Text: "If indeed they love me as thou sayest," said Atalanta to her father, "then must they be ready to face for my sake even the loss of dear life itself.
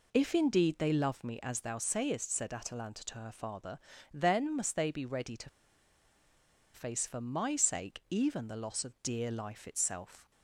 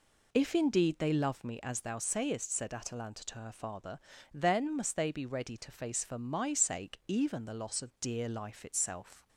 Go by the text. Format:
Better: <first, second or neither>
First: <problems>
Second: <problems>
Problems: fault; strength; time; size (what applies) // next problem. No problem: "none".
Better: second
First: pauses between "to" and "face"; strong; at 5.4 s; 1.2 s long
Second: none